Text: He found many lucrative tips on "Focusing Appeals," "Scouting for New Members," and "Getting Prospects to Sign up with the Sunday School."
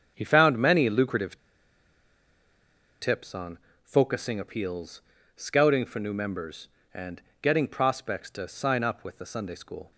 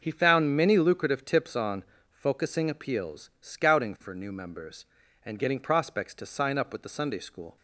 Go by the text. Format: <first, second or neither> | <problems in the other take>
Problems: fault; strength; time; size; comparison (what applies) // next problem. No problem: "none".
second | starts louder than the rest; strong; until 1.1 s; 7 dB; noticeable in the second // pauses between "lucrative" and "tips"; strong; at 1.3 s; 1.6 s long // pauses between "on" and "Focusing"; slight; at 3.5 s; 0.24 s long; slight in the second // pauses between "and" and "Getting"; slight; at 7.2 s; 0.22 s long